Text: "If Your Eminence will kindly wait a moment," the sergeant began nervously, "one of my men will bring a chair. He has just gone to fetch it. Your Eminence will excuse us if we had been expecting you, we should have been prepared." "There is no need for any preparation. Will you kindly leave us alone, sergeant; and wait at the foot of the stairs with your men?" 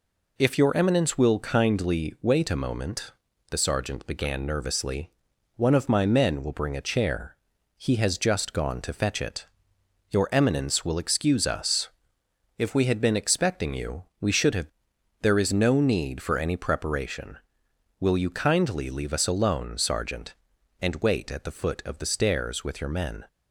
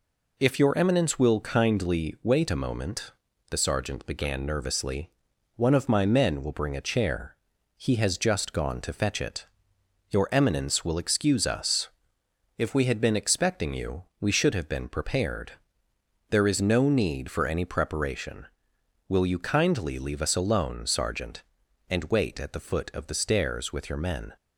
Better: second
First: pauses between "us" and "if"; noticeable; at 11.8 s; 0.70 s long // skips "been prepared"; at 14.9 s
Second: pauses between "us" and "if"; noticeable; at 11.8 s; 0.70 s long

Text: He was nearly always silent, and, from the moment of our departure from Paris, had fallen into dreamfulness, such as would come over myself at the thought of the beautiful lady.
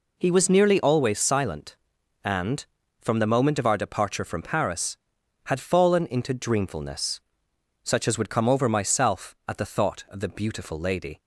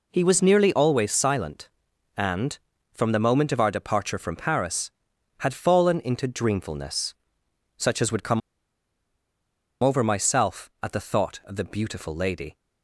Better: first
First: none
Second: pauses between "come" and "over"; strong; at 8.4 s; 1.4 s long

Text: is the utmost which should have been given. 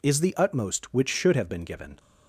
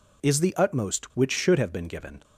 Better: neither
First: none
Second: none

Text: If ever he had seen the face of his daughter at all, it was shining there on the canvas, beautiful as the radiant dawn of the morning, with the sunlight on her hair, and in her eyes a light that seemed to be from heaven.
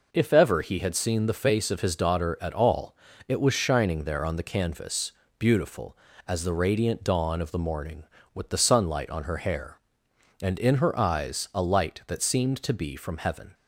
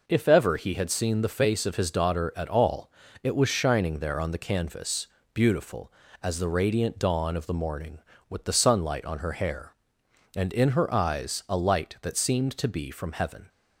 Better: neither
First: none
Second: none

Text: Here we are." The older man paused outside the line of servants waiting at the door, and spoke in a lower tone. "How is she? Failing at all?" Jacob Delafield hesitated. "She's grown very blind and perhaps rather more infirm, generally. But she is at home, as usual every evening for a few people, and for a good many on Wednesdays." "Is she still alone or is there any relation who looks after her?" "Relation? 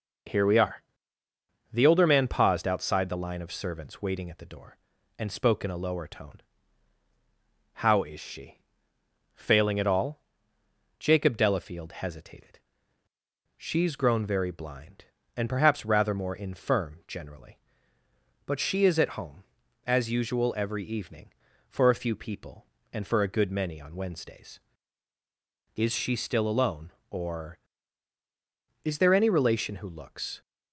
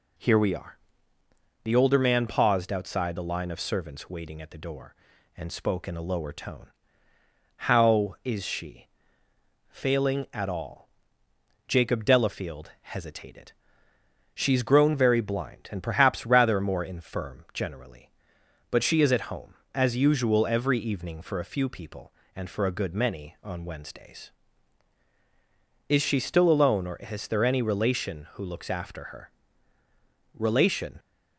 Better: second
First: stops before "after her Relation"; at 30.4 s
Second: none

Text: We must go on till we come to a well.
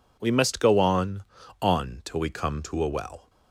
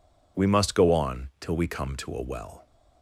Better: second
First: says "on" twice; at 1.6 s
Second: none

